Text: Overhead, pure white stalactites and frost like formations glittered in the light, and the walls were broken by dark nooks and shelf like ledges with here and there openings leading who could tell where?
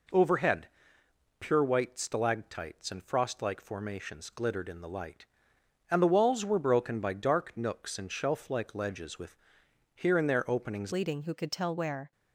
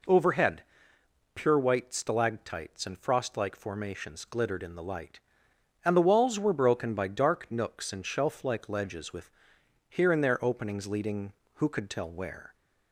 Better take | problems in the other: second | pauses between "with" and "here"; noticeable; at 9.3 s; 0.60 s long; noticeable in the second // changes voice at "leading"; from 10.9 s on; 1.2 s long

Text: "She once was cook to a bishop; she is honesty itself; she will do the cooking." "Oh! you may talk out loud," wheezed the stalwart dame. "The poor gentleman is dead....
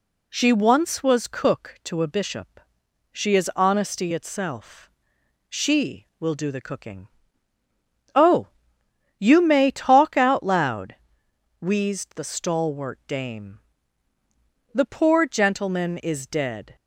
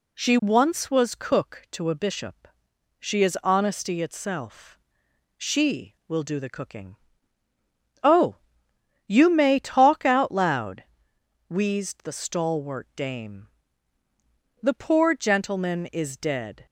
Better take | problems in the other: neither | none

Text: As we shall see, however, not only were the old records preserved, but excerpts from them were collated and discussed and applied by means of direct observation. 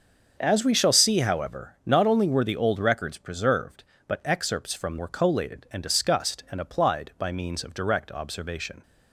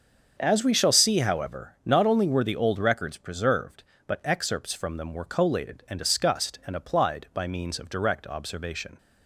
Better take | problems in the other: second | starts louder than the rest; until 1.4 s; 6.5 dB; also in the second // skips "them"; at 4.9 s

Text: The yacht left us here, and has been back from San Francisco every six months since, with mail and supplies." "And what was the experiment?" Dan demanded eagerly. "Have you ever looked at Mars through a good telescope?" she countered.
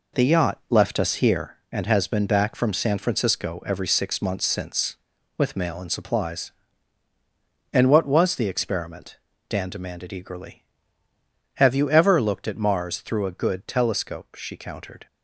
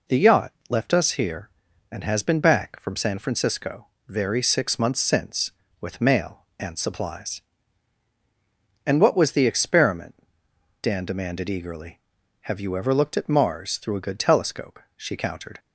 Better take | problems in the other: first | pauses between "yacht" and "left"; slight; at 0.5 s; 0.16 s long // says "very" for "every"; at 4.0 s

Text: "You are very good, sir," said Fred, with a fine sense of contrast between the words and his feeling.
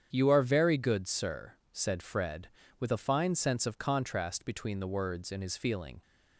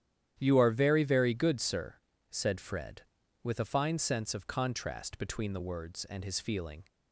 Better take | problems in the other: first | starts louder than the rest; strong; until 1.4 s; 11 dB; strong in the first // says "very" twice; at 1.0 s

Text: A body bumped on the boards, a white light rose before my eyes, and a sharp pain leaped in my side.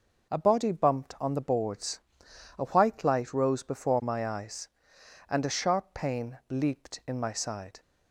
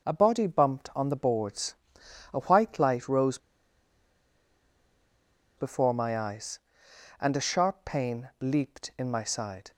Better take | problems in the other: first | pauses between "rose" and "before"; strong; at 3.3 s; 2.2 s long

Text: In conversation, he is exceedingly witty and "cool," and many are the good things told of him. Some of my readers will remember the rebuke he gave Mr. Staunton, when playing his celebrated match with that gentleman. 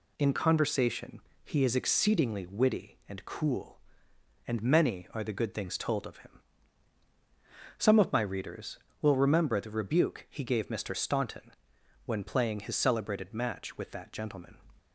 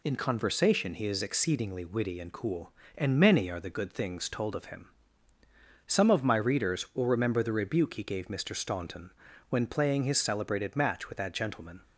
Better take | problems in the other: neither | none

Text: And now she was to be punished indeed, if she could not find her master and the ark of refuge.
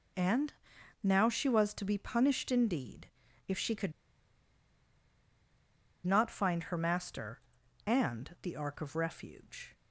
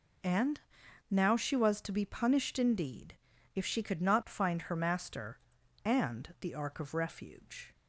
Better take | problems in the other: second | pauses between "And" and "now"; noticeable; at 0.5 s; 0.50 s long; noticeable in the second // pauses between "could" and "not"; strong; at 3.9 s; 2.1 s long

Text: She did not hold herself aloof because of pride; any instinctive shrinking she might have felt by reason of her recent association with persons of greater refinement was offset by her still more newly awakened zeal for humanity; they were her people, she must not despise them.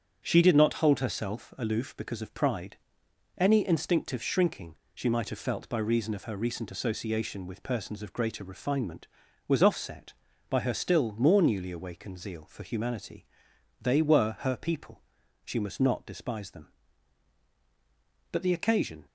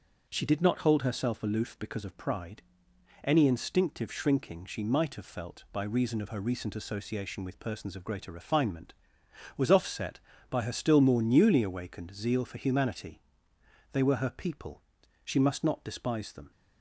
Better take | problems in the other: second | starts louder than the rest; strong; until 1.2 s; 8 dB // pauses between "shrinking" and "she"; slight; at 4.7 s; 0.18 s long // goes on to say "But the occasion"; noticeable; from 18.2 s on; 0.76 s long

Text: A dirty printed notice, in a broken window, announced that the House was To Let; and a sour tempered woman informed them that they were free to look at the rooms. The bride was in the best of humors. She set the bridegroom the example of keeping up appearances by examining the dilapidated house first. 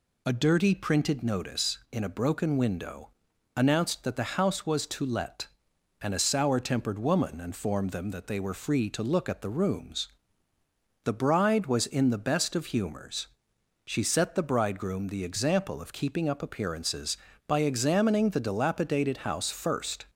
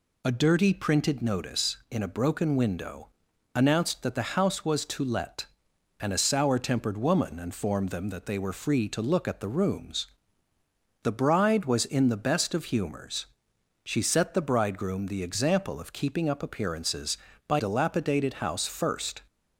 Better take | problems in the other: first | skips "examining the"; at 17.5 s

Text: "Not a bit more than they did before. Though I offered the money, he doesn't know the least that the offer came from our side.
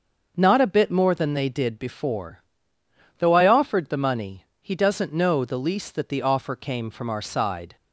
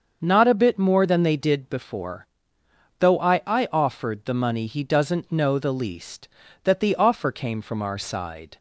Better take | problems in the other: first | starts louder than the rest; until 1.2 s; 6.5 dB; also in the first // says "I" twice; at 3.4 s

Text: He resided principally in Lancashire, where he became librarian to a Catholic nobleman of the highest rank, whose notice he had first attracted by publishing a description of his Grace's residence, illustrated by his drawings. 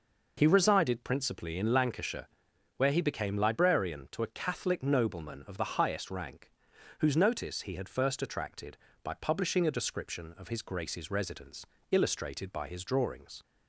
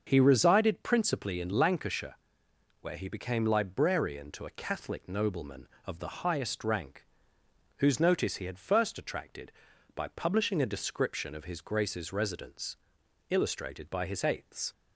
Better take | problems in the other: first | starts louder than the rest; until 1.0 s; 6.5 dB // says "eighths" for "drawings"; at 14.2 s

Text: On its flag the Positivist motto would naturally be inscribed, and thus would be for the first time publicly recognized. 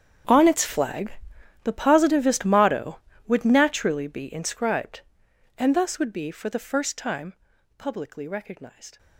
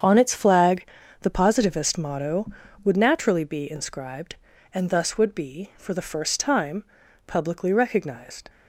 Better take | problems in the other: second | gets quieter; strong; throughout; 18.5 dB // starts louder than the rest; strong; until 1.7 s; 8 dB; strong in the second // pauses between "flag" and "the"; noticeable; at 1.1 s; 0.50 s long; also in the second // pauses between "time" and "publicly"; at 7.3 s; 0.44 s long; also in the second

